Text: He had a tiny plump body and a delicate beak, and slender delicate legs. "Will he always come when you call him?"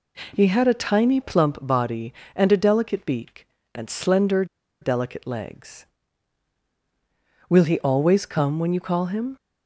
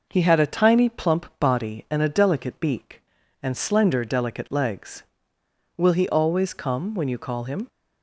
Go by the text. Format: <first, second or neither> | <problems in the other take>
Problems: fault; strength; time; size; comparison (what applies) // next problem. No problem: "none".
second | pauses between "slender" and "delicate"; at 4.4 s; 0.36 s long